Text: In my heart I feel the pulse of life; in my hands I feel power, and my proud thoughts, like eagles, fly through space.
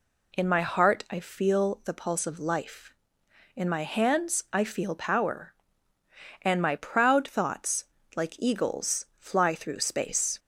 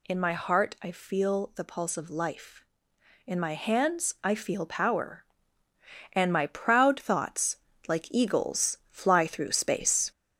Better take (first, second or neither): first